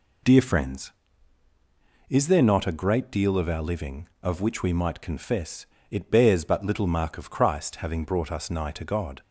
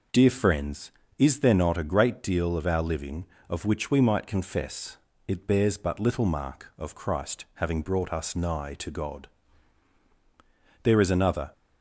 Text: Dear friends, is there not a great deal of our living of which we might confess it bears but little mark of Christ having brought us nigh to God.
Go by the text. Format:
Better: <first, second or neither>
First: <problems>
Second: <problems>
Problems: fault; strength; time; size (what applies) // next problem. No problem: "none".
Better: first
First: pauses between "confess" and "it"; slight; at 5.6 s; 0.24 s long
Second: pauses between "confess" and "it"; slight; at 4.9 s; 0.30 s long // goes on to say "There is another"; noticeable; from 10.8 s on; 0.70 s long